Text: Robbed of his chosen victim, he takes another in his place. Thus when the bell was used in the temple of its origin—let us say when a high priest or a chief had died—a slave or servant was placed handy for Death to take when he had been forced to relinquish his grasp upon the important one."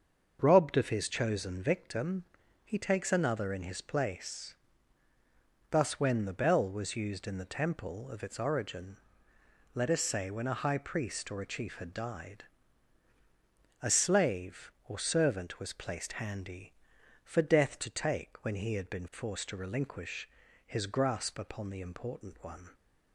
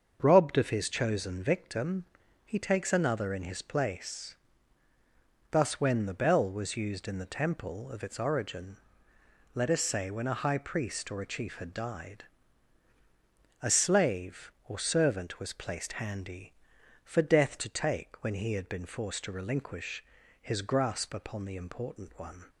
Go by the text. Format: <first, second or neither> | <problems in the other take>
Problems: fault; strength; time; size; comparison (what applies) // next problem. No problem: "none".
neither | starts louder than the rest; the same in both // pauses between "relinquish" and "his"; the same in both